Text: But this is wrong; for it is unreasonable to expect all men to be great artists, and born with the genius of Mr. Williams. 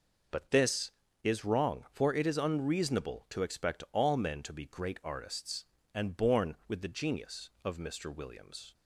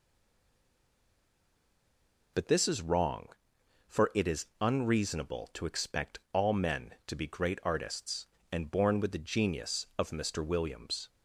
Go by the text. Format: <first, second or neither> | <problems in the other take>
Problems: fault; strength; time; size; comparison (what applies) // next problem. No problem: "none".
first | stays silent before the first word; until 2.3 s; 2.3 s long